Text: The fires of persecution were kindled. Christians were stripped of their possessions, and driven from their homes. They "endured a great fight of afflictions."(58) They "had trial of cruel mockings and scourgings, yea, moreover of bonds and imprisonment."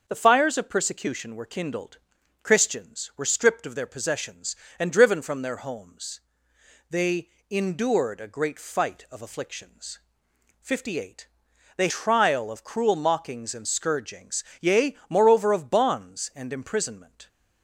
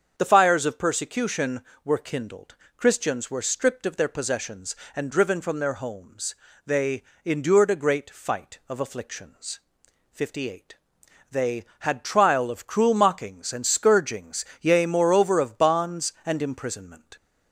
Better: second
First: starts louder than the rest; until 1.0 s; 6.5 dB // pauses between "They" and "endured"; slight; at 7.2 s; 0.20 s long // skips "had"; at 11.8 s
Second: starts louder than the rest; until 1.1 s; 7 dB // pauses between "They" and "endured"; slight; at 7.0 s; 0.22 s long

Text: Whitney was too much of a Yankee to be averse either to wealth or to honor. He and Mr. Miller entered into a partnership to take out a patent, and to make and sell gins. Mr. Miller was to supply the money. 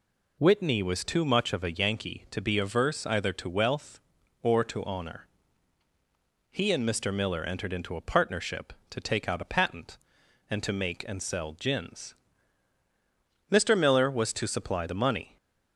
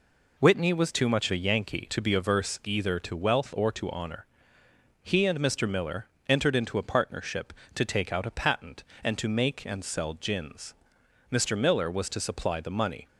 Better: first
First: none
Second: skips "of"; at 1.3 s // pauses between "Miller" and "entered"; slight; at 6.0 s; 0.20 s long

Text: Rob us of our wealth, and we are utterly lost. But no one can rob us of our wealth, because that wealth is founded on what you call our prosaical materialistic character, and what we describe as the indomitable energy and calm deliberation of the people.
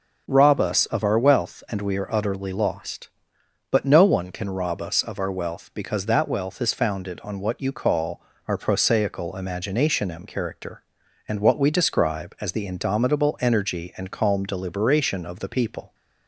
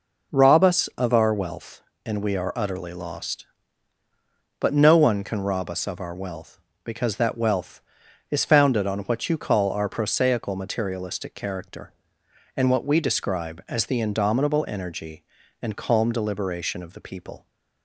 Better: second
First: pauses between "call" and "our"; slight; at 8.1 s; 0.28 s long // says "imaginationem" for "materialistic"; at 9.3 s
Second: none

